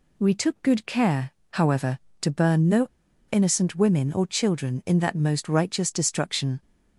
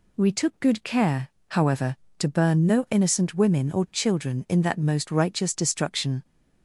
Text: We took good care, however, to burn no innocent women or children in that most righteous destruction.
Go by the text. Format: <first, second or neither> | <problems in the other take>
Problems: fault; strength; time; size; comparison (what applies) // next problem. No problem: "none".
second | pauses between "no" and "innocent"; at 2.8 s; 0.44 s long